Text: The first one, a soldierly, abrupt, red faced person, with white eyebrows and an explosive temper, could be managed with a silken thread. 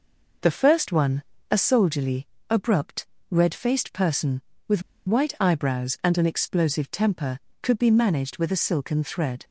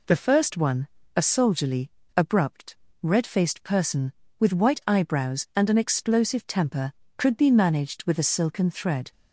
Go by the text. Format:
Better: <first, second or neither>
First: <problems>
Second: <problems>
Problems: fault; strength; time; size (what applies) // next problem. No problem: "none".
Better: second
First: pauses between "with" and "white"; slight; at 4.8 s; 0.27 s long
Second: none